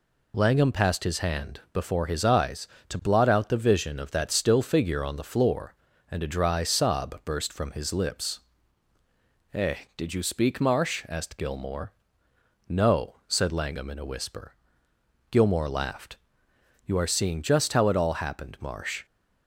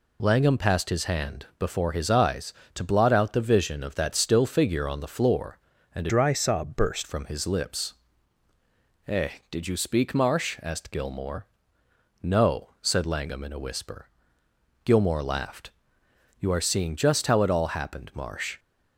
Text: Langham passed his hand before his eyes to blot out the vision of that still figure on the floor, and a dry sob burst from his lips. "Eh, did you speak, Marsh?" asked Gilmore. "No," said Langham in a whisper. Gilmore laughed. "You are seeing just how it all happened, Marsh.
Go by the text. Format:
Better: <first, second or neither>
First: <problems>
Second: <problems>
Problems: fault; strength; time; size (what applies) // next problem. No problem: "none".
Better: first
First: none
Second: changes voice from "dry" to "burst"; from 6.0 to 7.0 s; 1.0 s long